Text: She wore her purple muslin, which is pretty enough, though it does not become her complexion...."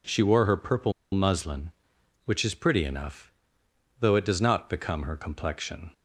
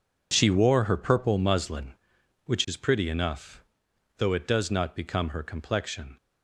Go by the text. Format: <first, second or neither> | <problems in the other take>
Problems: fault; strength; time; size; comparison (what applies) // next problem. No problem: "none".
second | pauses between "purple" and "muslin"; slight; at 0.9 s; 0.20 s long